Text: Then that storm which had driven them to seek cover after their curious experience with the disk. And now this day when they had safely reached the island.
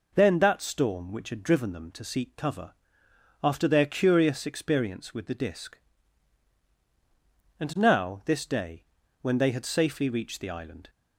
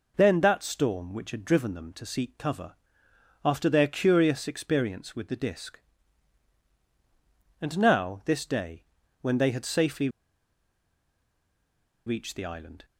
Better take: first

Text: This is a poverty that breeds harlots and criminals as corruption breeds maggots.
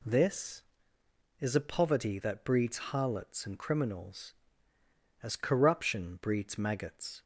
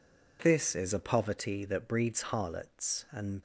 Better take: first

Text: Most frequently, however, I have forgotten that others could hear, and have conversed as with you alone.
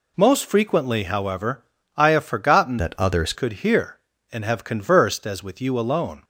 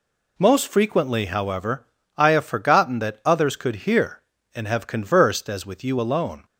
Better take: second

